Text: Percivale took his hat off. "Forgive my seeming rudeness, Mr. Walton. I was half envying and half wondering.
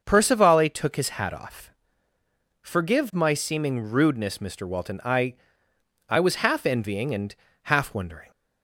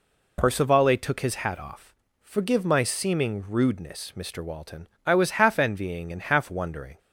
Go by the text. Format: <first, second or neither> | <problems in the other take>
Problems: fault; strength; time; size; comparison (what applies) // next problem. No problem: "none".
second | starts louder than the rest; until 1.0 s; 6.5 dB // says "I" twice; at 6.0 s // pauses between "and" and "half"; slight; at 7.3 s; 0.30 s long